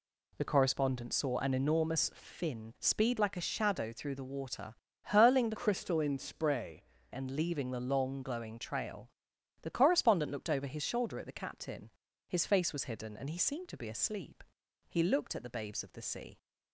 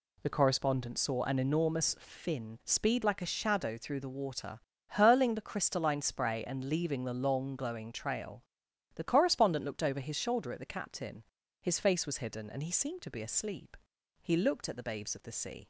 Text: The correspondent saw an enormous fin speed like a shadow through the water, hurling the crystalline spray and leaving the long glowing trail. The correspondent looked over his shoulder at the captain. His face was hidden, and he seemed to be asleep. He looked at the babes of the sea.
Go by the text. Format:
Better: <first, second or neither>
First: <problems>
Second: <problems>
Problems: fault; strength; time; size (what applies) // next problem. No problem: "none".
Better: second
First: changes voice from "crystalline" to "spray"; from 5.5 to 6.8 s; 1.3 s long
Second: none